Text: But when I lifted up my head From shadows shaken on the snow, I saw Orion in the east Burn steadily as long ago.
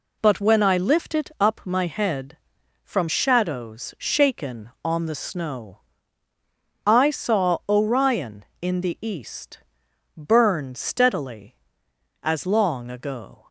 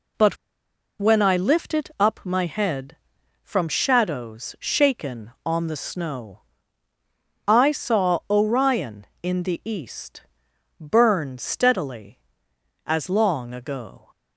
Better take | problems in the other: first | pauses between "But" and "when"; noticeable; at 0.3 s; 0.63 s long // pauses between "east" and "Burn"; noticeable; at 10.2 s; 0.58 s long; noticeable in the first

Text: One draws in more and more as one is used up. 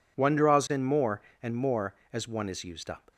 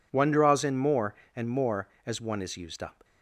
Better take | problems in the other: neither | none

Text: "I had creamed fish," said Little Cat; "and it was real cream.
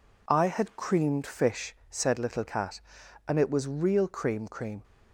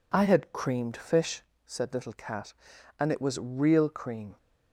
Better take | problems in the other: second | says "cream" twice; at 4.4 s

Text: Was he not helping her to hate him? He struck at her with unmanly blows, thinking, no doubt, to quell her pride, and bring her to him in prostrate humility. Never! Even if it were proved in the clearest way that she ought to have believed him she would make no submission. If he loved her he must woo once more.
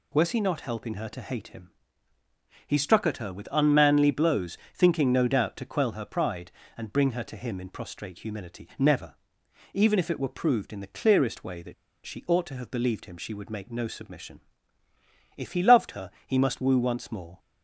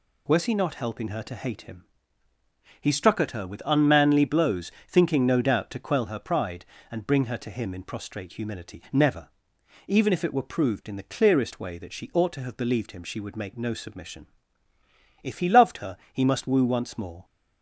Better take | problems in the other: second | pauses between "that" and "she"; slight; at 11.7 s; 0.32 s long // pauses between "her" and "he"; slight; at 16.1 s; 0.16 s long; slight in the second

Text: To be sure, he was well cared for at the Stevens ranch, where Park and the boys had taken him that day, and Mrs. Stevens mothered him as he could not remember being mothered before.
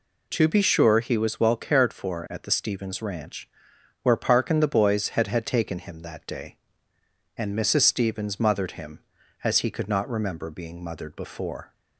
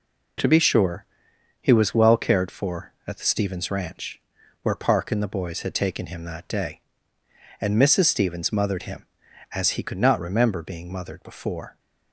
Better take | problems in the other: second | says "had" twice; at 5.2 s

